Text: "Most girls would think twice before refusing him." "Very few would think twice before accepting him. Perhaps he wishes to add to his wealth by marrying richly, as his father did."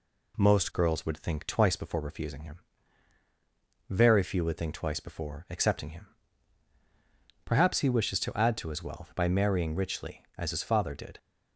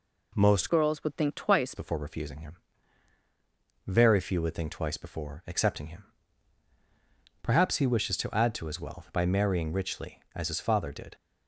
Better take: first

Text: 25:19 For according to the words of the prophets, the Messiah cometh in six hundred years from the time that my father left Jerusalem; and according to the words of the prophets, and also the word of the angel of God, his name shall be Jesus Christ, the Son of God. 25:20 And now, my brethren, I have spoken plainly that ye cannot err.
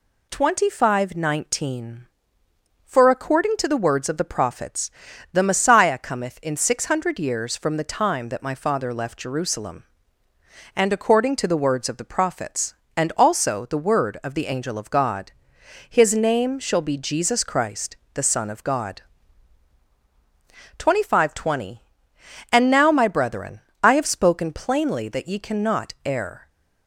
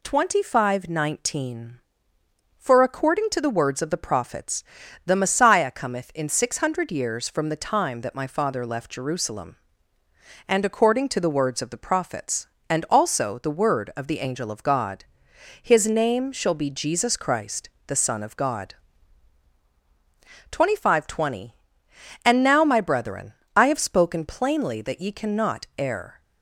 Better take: neither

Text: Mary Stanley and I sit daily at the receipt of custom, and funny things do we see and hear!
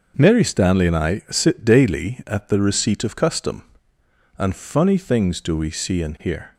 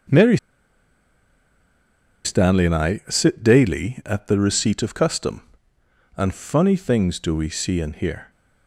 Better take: first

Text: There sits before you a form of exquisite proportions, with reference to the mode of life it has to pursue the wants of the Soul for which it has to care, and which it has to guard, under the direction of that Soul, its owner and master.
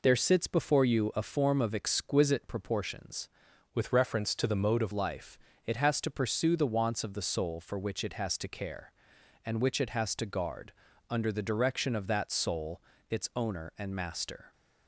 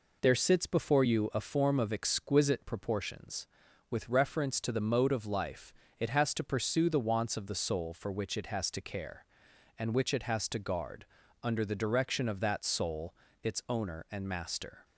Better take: second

